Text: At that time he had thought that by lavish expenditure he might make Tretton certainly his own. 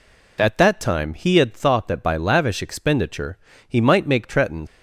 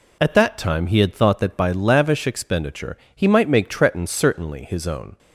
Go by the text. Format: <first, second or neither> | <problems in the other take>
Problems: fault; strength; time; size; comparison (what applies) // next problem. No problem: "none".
second | pauses between "expenditure" and "he"; slight; at 3.3 s; 0.30 s long; slight in the second // stops before "certainly his own"; at 4.6 s